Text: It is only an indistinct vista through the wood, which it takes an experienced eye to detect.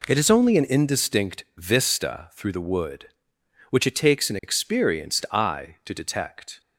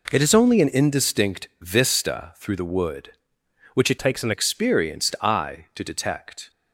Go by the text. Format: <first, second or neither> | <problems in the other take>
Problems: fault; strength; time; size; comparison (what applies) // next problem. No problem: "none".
first | changes voice from "takes" to "an"; from 3.9 to 4.3 s; 0.4 s long